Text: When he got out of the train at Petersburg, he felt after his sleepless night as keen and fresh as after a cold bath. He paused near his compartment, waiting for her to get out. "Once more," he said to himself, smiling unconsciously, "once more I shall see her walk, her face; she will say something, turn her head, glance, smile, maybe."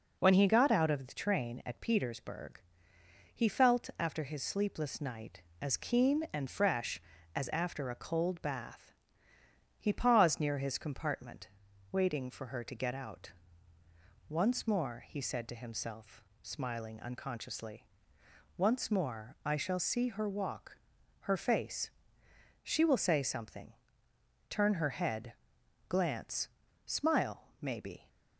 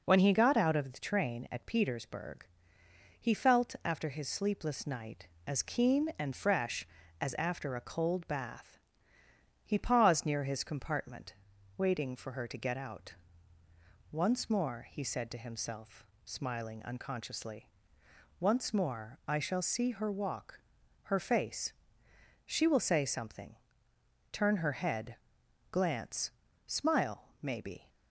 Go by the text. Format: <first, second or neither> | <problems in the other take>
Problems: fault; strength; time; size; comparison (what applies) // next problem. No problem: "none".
neither | none